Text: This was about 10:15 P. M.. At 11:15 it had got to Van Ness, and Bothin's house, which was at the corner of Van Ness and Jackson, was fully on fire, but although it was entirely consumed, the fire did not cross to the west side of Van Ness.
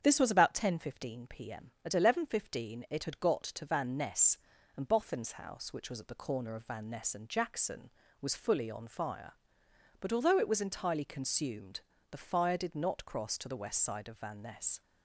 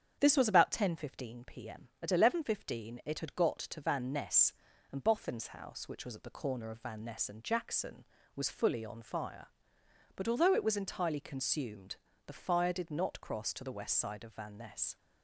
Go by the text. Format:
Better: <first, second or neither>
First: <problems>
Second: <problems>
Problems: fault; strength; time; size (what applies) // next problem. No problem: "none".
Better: neither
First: starts louder than the rest; strong; until 1.0 s; 8 dB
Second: starts louder than the rest; strong; until 1.2 s; 8 dB